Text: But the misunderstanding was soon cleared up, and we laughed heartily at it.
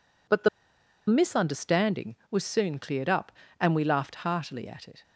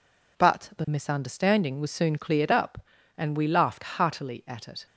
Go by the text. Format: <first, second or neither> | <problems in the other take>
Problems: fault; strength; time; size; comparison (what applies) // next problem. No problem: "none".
second | pauses between "the" and "misunderstanding"; noticeable; at 0.4 s; 0.60 s long